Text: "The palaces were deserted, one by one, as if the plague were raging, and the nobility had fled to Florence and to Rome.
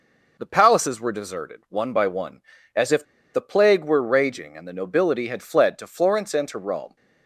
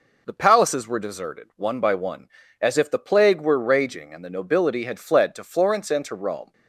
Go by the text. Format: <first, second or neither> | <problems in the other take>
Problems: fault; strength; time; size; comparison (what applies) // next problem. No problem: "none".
second | pauses between "if" and "the"; slight; at 3.0 s; 0.30 s long